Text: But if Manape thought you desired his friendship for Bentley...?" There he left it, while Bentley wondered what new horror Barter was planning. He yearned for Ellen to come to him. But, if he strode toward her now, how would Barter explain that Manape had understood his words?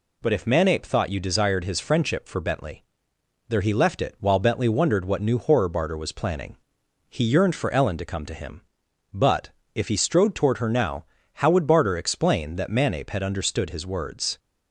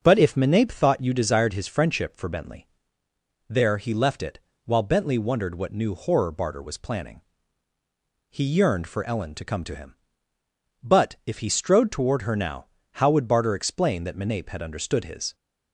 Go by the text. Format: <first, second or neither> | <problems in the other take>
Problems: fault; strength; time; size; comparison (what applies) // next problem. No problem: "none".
first | starts louder than the rest; until 1.0 s; 6 dB // stops before "words"; at 15.3 s